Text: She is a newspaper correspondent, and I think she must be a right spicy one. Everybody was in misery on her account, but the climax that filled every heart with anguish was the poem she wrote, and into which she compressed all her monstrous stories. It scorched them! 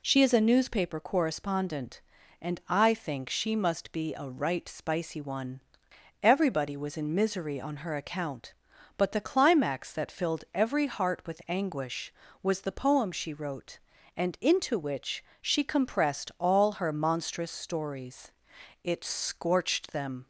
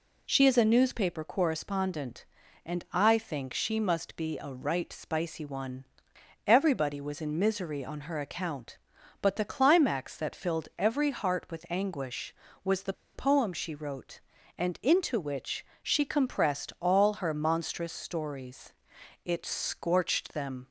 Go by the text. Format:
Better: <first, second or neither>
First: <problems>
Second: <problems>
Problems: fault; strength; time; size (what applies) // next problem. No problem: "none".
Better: first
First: pauses between "which" and "she"; slight; at 15.2 s; 0.18 s long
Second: pauses between "the" and "poem"; slight; at 12.9 s; 0.22 s long // pauses between "which" and "she"; slight; at 15.6 s; 0.18 s long